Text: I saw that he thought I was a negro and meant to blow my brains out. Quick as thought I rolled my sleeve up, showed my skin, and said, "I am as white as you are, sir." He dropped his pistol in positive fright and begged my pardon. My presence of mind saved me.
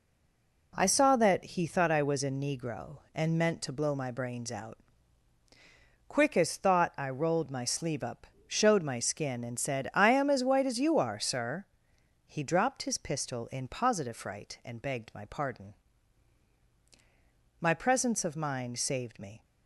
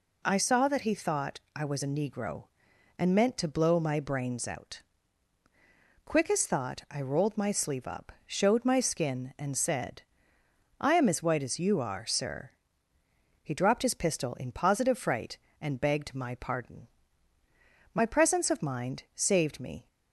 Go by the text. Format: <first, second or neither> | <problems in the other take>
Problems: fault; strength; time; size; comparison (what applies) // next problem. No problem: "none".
second | stays silent before the first word; slight; until 0.7 s; 0.7 s long